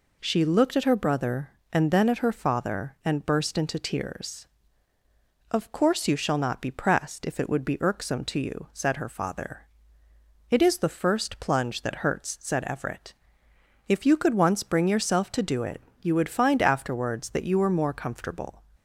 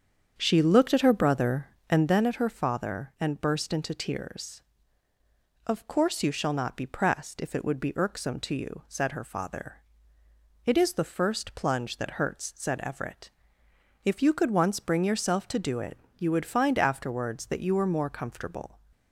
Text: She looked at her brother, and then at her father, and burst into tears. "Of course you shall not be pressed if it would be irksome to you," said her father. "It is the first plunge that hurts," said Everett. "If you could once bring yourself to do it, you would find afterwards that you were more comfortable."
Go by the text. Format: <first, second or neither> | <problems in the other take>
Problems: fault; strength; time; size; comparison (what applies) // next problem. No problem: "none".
first | starts louder than the rest; strong; until 2.2 s; 7.5 dB